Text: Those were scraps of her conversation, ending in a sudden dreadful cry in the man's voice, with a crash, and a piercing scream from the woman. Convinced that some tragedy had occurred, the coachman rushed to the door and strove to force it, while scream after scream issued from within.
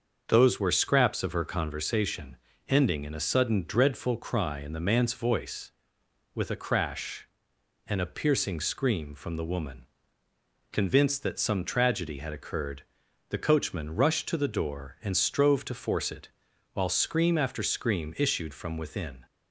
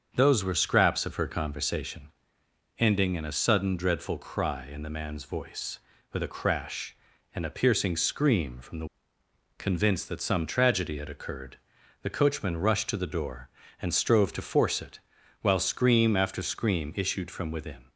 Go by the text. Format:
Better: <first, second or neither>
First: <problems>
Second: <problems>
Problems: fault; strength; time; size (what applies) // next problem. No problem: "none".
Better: first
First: starts louder than the rest; until 1.2 s; 6.5 dB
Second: starts louder than the rest; until 1.1 s; 6.5 dB // skips "woman"; at 9.2 s